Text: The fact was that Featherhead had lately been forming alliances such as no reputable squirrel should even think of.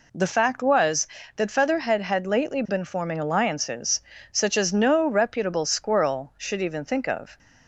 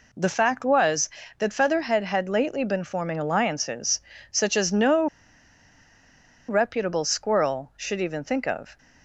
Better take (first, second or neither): first